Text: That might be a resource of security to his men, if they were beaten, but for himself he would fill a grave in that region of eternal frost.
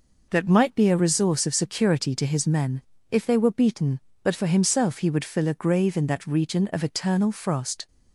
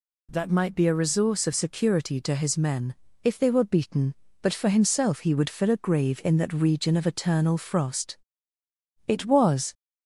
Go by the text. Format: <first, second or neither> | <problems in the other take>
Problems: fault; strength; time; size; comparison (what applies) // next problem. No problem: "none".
first | goes on to say "It was"; noticeable; from 9.0 s on; 0.66 s long